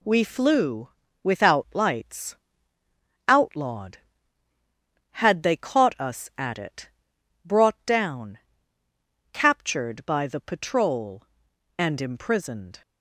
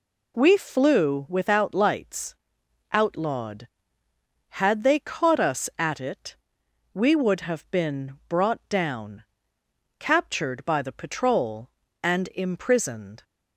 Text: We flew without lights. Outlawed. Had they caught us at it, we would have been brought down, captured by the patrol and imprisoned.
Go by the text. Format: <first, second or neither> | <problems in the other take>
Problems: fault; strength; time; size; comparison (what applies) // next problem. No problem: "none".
second | pauses between "flew" and "without"; slight; at 0.8 s; 0.32 s long // skips "we would have been"; at 7.1 s